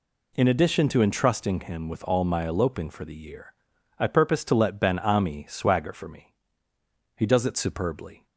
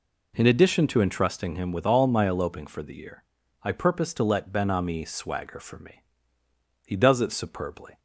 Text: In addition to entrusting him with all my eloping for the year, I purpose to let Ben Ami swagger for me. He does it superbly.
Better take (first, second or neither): neither